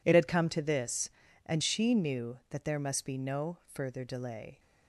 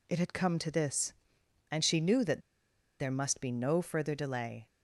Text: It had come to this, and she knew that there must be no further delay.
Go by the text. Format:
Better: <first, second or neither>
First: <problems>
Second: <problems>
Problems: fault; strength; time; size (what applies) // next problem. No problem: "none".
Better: first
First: none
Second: pauses between "that" and "there"; noticeable; at 2.4 s; 0.59 s long